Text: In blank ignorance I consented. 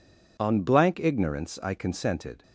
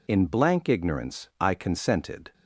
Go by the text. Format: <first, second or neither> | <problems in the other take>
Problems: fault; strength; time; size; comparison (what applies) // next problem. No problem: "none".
second | says "On" for "In"; at 0.4 s